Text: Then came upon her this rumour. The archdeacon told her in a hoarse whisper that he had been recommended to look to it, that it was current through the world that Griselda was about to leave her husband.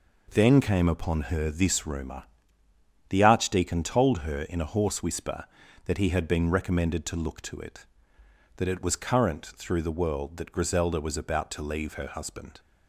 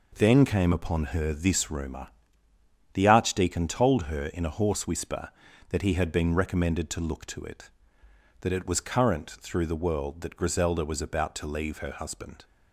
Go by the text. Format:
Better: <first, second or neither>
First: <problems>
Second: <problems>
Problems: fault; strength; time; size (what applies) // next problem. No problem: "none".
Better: neither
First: none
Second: none